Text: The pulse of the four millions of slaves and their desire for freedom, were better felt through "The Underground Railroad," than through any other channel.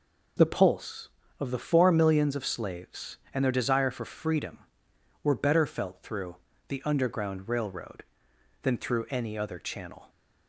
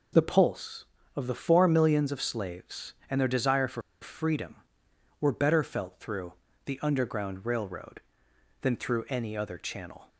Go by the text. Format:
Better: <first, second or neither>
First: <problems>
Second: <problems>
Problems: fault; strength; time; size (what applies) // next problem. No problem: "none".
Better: first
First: pauses between "through" and "The"; slight; at 6.3 s; 0.34 s long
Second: pauses between "for" and "freedom"; slight; at 3.8 s; 0.20 s long // pauses between "through" and "The"; slight; at 6.3 s; 0.34 s long